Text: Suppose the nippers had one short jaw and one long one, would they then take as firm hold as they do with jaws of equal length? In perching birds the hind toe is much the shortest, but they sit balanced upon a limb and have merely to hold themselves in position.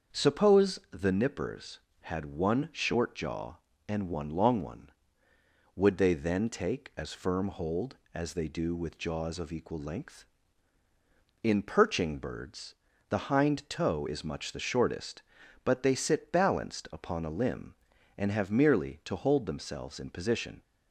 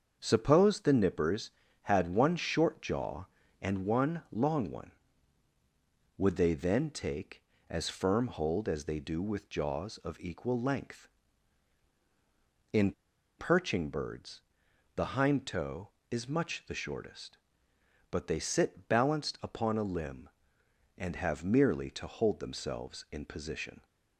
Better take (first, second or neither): first